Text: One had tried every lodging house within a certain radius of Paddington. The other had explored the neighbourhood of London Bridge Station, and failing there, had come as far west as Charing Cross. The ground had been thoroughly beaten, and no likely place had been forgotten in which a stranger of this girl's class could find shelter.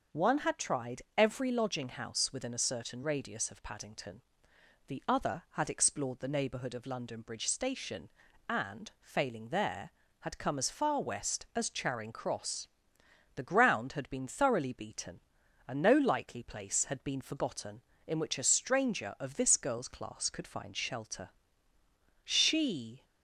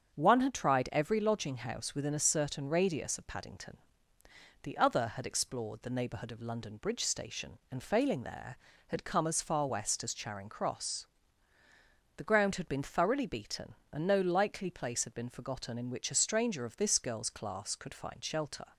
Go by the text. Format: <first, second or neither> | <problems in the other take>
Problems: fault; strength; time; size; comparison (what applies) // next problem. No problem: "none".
second | starts louder than the rest; until 1.2 s; 6.5 dB; strong in the second // goes on to say "She"; noticeable; from 22.2 s on; 0.80 s long